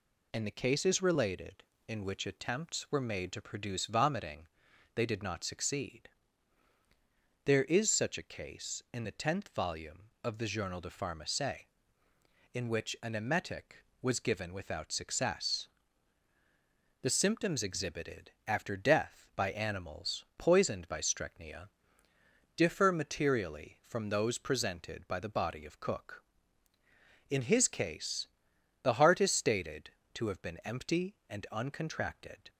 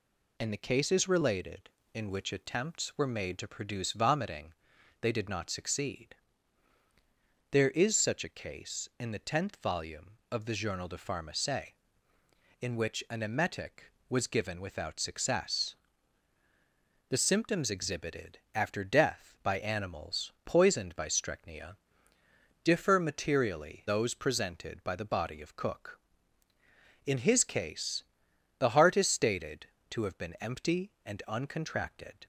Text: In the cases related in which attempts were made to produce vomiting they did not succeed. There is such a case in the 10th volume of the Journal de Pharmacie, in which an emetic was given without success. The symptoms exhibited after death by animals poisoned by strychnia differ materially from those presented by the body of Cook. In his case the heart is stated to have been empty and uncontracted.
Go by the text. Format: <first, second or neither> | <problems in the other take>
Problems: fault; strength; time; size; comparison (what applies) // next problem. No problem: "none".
first | pauses between "vomiting" and "they"; noticeable; at 4.5 s; 0.48 s long; noticeable in the first // pauses between "exhibited" and "after"; slight; at 18.3 s; 0.16 s long; slight in the first // pauses between "strychnia" and "differ"; noticeable; at 21.7 s; 0.86 s long; noticeable in the first // skips "from"; at 23.8 s // pauses between "case" and "the"; noticeable; at 28.0 s; 0.56 s long; noticeable in the first